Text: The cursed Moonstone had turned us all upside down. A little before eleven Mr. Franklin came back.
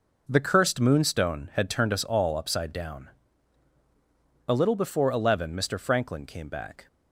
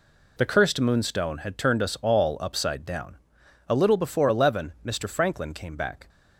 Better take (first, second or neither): neither